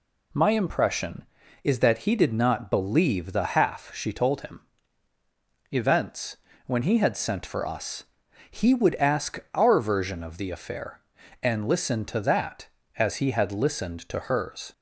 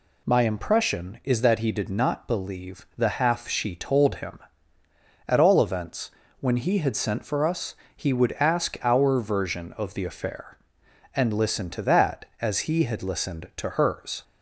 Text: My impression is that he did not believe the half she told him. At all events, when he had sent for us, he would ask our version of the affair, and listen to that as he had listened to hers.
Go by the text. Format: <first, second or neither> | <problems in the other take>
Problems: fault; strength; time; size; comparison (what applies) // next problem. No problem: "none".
second | skips "At all"; at 5.1 s // pauses between "ask" and "our"; slight; at 9.3 s; 0.16 s long